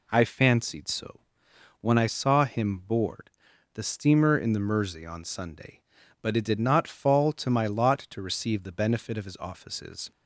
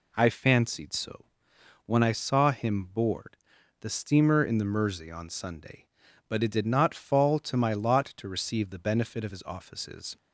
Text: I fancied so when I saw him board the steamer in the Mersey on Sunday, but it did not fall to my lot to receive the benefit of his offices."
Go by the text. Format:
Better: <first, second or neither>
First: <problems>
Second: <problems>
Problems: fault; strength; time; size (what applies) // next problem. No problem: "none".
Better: neither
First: pauses between "so" and "when"; noticeable; at 1.2 s; 0.60 s long // pauses between "board" and "the"; noticeable; at 3.2 s; 0.46 s long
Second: pauses between "so" and "when"; noticeable; at 1.2 s; 0.60 s long // pauses between "board" and "the"; noticeable; at 3.3 s; 0.46 s long